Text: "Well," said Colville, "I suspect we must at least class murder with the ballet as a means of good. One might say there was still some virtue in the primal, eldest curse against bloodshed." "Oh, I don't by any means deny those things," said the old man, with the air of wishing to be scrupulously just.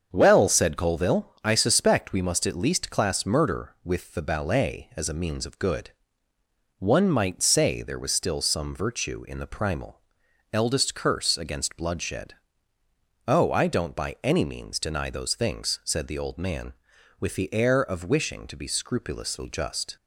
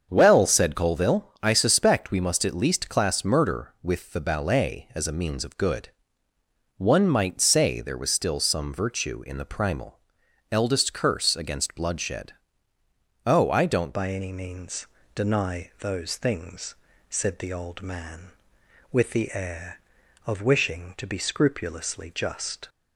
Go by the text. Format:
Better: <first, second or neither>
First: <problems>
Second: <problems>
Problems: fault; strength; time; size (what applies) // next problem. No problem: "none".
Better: first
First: starts louder than the rest; until 1.1 s; 7 dB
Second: starts louder than the rest; until 1.1 s; 7 dB // changes voice at "by"; from 13.9 s on; 8.7 s long // pauses between "means" and "deny"; slight; at 14.8 s; 0.26 s long